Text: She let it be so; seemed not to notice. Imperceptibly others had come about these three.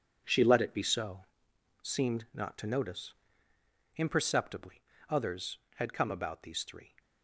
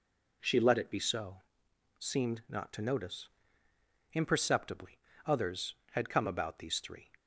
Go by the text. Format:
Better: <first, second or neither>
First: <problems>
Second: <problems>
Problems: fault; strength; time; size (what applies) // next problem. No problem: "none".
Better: second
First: gets quieter; strong; throughout; 9.5 dB // pauses between "Imperceptibly" and "others"; slight; at 4.8 s; 0.28 s long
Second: pauses between "Imperceptibly" and "others"; slight; at 4.9 s; 0.28 s long